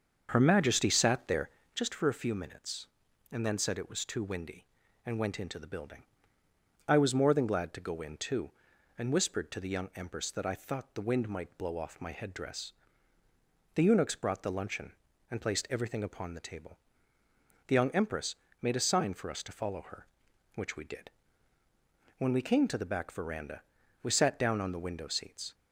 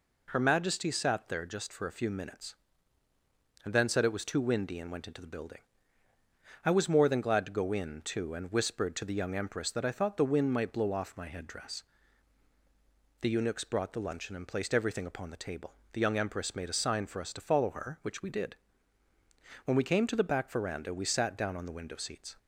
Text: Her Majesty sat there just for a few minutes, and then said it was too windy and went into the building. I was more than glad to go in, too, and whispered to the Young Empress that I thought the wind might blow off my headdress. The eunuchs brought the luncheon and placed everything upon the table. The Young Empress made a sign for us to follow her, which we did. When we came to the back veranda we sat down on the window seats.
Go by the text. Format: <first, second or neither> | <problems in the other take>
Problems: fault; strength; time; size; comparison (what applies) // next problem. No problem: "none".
second | starts louder than the rest; until 2.0 s; 6.5 dB // pauses between "there" and "just"; slight; at 1.4 s; 0.24 s long // pauses between "Empress" and "made"; slight; at 18.3 s; 0.26 s long // pauses between "veranda" and "we"; at 23.6 s; 0.42 s long